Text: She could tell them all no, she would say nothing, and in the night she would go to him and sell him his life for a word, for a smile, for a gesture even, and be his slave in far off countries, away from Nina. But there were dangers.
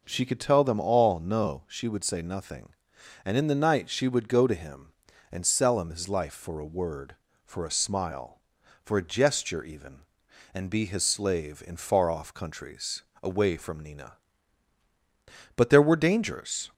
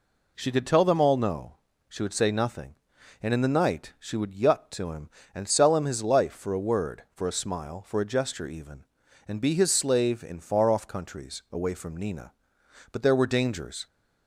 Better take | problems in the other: first | says "yut" for "go"; at 4.3 s

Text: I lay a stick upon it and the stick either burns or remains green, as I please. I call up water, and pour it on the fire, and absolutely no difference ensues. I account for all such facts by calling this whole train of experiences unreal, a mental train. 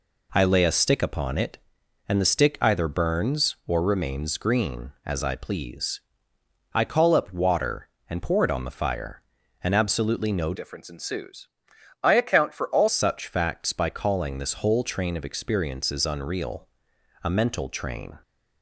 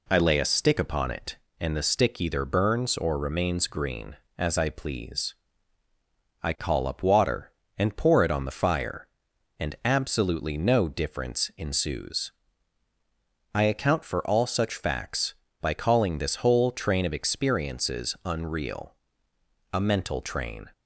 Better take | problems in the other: second | changes voice from "difference" to "all"; from 10.5 to 12.8 s; 2.3 s long

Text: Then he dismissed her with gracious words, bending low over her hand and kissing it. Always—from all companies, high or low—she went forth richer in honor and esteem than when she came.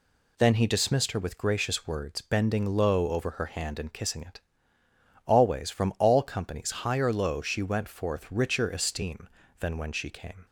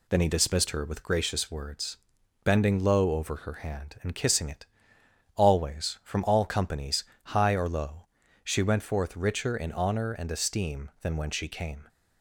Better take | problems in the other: second | skips "in honor and"; at 8.6 s

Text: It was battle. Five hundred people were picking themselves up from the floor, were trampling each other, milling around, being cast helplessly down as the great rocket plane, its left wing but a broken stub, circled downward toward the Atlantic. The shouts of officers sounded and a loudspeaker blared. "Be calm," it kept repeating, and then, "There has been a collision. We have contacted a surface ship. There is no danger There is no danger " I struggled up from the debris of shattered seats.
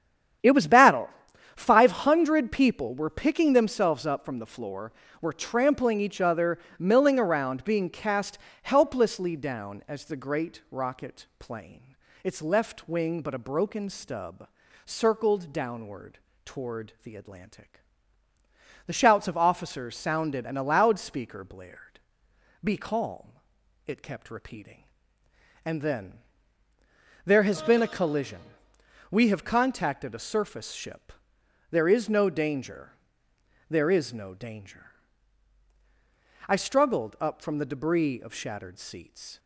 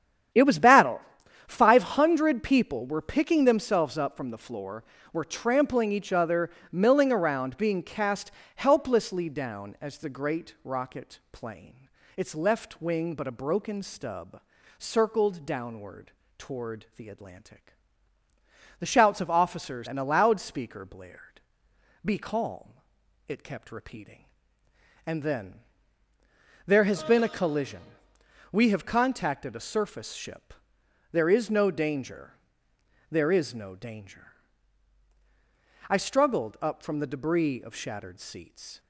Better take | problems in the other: first | starts louder than the rest; strong; until 1.8 s; 9.5 dB; strong in the first // pauses between "cast" and "helplessly"; slight; at 8.3 s; 0.24 s long; slight in the first // pauses between "downward" and "toward"; slight; at 16.1 s; 0.26 s long; slight in the first // skips "sounded"; at 19.8 s // pauses between "danger" and "There"; noticeable; at 32.3 s; 0.76 s long; noticeable in the first

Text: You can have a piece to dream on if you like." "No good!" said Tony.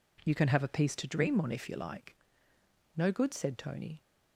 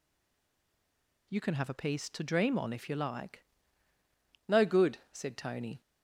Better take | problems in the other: first | stays silent before the first word; noticeable; until 1.2 s; 1.2 s long

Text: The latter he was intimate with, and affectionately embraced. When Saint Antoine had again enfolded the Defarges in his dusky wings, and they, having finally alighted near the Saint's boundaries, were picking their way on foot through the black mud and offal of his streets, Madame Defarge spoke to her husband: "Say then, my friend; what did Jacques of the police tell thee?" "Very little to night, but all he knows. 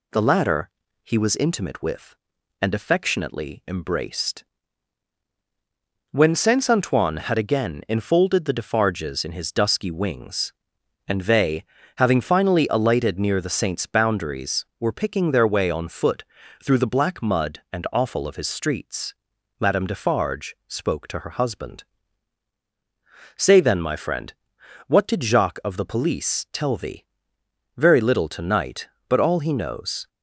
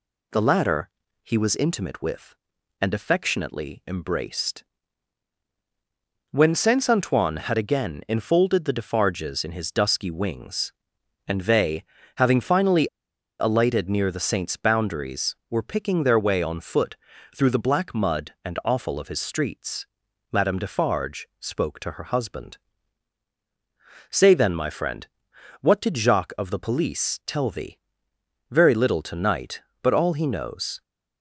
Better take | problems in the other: first | pauses between "latter" and "he"; slight; at 0.8 s; 0.34 s long; slight in the first // pauses between "finally" and "alighted"; noticeable; at 12.8 s; 0.54 s long // pauses between "foot" and "through"; at 16.9 s; 0.40 s long; also in the first

